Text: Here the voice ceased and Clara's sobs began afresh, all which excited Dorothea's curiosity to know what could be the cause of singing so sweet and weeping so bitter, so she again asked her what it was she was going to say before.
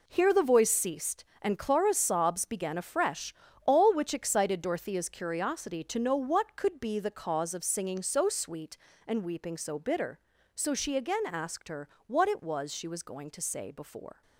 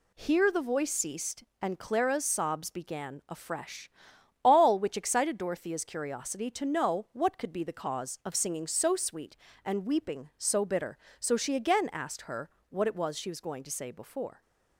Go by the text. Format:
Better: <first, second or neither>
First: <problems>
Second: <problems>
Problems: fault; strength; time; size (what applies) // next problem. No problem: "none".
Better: second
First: gets quieter; strong; throughout; 10 dB // pauses between "her" and "what"; slight; at 11.8 s; 0.18 s long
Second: pauses between "her" and "what"; slight; at 12.4 s; 0.20 s long